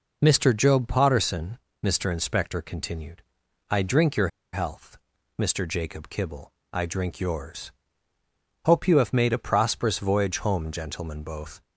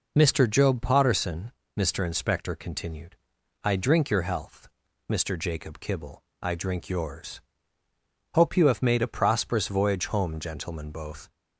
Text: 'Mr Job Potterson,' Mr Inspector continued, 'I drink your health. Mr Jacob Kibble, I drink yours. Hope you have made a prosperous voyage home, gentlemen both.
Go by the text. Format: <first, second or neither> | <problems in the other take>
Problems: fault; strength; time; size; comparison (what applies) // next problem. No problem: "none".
second | pauses between "your" and "health"; slight; at 4.2 s; 0.25 s long